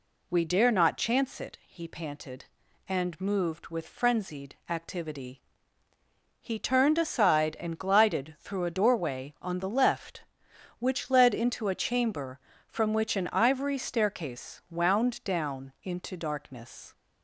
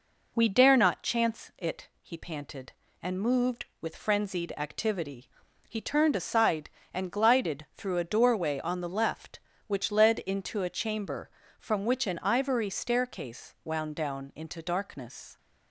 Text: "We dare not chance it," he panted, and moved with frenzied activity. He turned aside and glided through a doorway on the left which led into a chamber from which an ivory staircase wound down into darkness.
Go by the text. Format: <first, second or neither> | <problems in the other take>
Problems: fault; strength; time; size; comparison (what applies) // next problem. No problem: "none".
neither | none